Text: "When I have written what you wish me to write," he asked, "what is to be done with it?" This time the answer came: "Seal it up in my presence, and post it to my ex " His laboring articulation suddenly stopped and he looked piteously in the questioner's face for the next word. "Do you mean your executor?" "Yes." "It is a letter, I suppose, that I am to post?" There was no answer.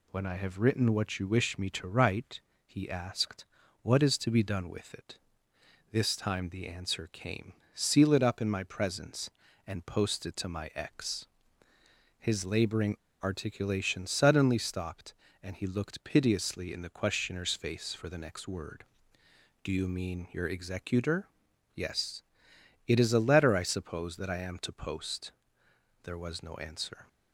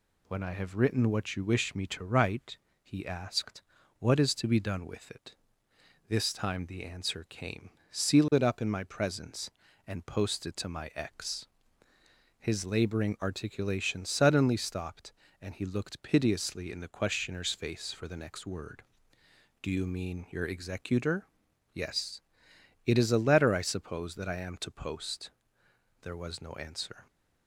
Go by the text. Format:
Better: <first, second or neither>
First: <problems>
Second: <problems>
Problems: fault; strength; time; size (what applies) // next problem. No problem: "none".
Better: second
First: pauses between "laboring" and "articulation"; slight; at 12.9 s; 0.27 s long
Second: none